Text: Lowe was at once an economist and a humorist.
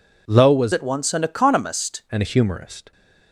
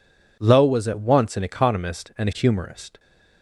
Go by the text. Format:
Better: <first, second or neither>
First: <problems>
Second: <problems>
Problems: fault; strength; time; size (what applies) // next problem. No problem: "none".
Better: second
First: changes voice from "at" to "economist"; from 0.7 to 2.0 s; 1.3 s long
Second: none